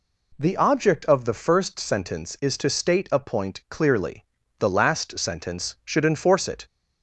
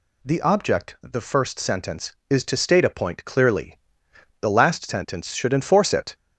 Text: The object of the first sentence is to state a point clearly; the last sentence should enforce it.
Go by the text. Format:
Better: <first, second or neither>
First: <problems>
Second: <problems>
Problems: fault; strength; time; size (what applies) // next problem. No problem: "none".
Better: first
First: none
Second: skips "of"; at 0.9 s